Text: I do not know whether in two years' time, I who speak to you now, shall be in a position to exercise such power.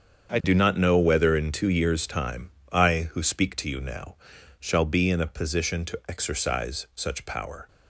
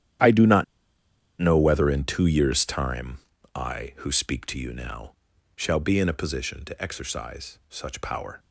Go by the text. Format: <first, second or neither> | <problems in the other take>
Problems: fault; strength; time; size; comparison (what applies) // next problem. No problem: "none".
first | starts louder than the rest; strong; until 2.0 s; 10.5 dB; strong in the first // pauses between "not" and "know"; noticeable; at 0.6 s; 0.76 s long